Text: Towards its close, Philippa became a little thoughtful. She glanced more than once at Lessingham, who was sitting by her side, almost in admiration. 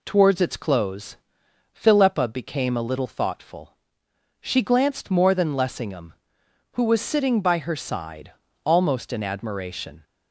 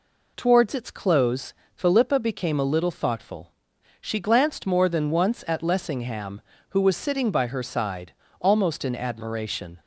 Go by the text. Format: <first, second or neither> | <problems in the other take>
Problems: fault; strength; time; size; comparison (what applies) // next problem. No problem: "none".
second | skips "once at"; at 5.5 s